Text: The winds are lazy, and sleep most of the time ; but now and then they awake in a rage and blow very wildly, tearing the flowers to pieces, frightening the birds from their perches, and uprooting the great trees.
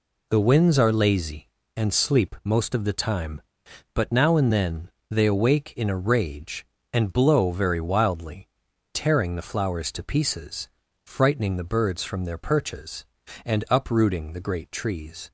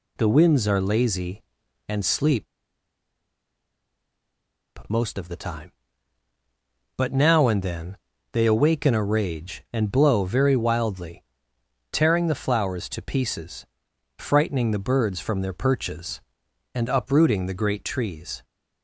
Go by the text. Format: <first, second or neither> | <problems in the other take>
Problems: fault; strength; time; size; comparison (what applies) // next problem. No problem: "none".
first | pauses between "sleep" and "most"; strong; at 2.4 s; 2.4 s long // pauses between "then" and "they"; at 7.9 s; 0.38 s long; slight in the first